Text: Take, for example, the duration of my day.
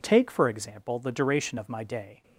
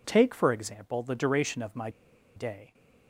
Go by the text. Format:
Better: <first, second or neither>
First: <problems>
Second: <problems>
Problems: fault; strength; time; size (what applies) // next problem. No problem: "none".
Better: first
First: none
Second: pauses between "my" and "day"; noticeable; at 1.8 s; 0.47 s long